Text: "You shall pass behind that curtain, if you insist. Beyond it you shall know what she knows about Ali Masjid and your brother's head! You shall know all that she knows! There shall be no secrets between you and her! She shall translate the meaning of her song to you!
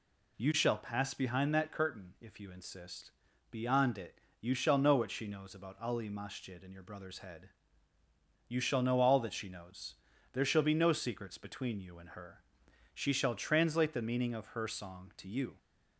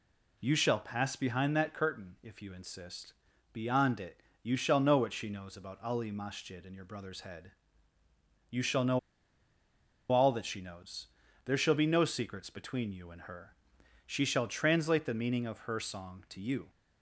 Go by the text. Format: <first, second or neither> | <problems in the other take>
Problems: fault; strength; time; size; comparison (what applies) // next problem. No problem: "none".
first | pauses between "it" and "you"; slight; at 4.2 s; 0.22 s long; slight in the first // pauses between "know" and "all"; at 8.9 s; 1.1 s long